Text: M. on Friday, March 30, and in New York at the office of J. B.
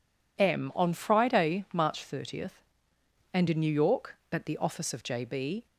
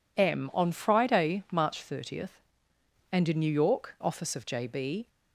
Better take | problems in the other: first | skips "at the"; at 3.9 s

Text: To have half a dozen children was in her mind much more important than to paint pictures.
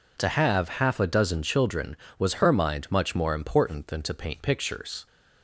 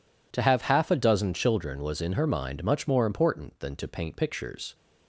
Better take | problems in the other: second | skips "in"; at 2.3 s

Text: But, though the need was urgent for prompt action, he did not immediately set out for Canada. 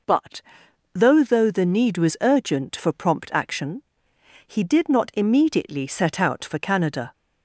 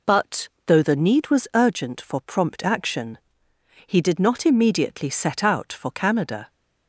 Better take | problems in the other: second | says "though" twice; at 1.2 s

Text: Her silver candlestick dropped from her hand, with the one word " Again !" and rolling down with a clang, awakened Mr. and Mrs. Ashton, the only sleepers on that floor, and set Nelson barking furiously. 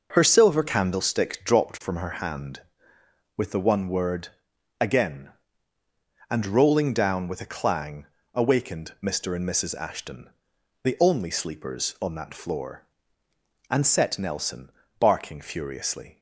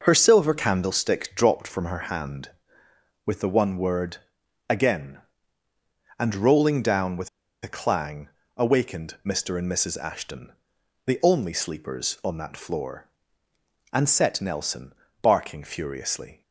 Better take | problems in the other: first | starts louder than the rest; until 1.0 s; 6 dB; also in the first // pauses between "with" and "a"; slight; at 7.2 s; 0.34 s long // pauses between "Nelson" and "barking"; slight; at 14.9 s; 0.30 s long; slight in the first

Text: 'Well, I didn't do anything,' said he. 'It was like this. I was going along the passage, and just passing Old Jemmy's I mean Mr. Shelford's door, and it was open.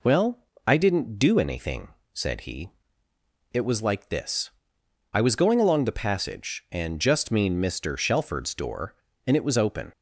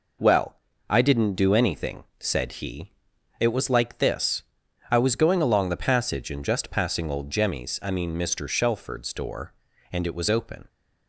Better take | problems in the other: second | skips "passing Old Jemmy's I"; at 7.3 s

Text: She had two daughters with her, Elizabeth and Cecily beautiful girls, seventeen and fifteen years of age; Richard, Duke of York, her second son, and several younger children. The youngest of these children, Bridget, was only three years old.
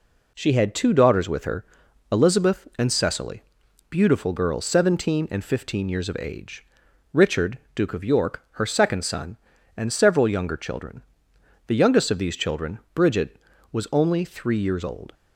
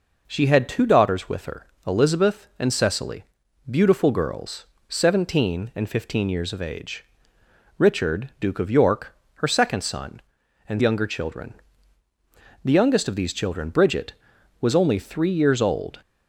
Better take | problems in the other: first | pauses between "Cecily" and "beautiful"; noticeable; at 3.2 s; 0.46 s long; noticeable in the first // skips "several"; at 10.8 s

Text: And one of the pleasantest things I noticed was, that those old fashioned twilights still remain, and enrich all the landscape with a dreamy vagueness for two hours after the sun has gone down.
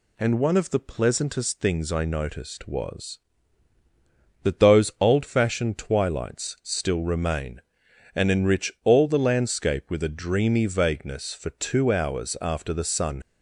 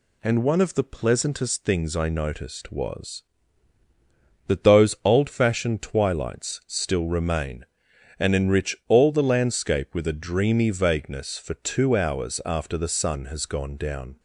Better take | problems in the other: second | stops before "has gone down"; at 13.2 s

